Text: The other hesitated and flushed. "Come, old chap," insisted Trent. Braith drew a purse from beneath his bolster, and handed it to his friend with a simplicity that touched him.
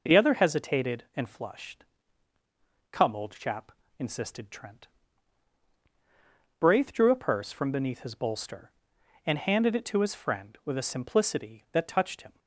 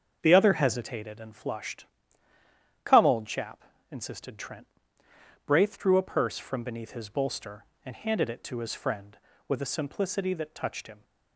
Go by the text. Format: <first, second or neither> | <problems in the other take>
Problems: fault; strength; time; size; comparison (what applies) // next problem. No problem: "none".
first | starts louder than the rest; until 1.3 s; 6.5 dB